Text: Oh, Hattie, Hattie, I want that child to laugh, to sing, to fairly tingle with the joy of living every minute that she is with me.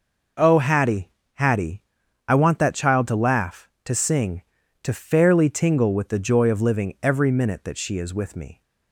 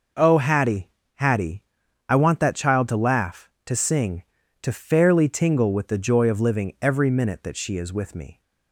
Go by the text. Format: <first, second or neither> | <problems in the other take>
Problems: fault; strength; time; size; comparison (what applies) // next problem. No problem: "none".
neither | none